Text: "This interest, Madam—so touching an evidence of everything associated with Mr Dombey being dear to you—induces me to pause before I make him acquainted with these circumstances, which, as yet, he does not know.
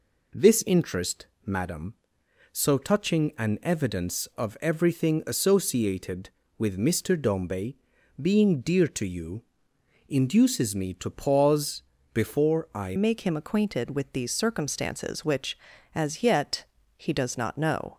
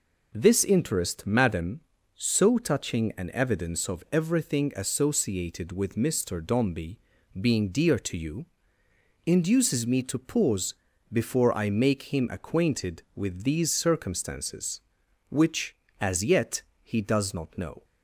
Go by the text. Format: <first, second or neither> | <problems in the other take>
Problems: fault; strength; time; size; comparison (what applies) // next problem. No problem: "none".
second | pauses between "Dombey" and "being"; at 7.7 s; 0.42 s long; also in the second // pauses between "pause" and "before"; slight; at 11.8 s; 0.30 s long; slight in the second // changes voice at "make"; from 12.9 s on; 5.0 s long